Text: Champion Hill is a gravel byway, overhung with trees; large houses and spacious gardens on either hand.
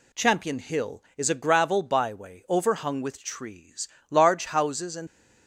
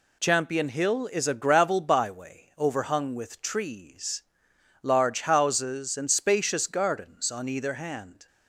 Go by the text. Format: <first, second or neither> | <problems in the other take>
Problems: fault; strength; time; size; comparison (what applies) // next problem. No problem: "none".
second | stops before "spacious gardens on either hand"; at 5.0 s